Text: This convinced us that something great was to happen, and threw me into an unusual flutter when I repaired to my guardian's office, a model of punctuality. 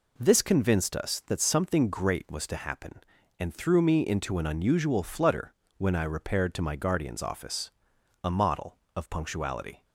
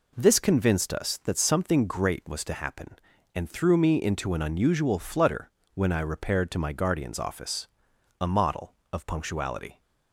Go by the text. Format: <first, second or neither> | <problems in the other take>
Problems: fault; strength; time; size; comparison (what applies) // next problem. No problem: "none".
neither | pauses between "flutter" and "when"; slight; the same in both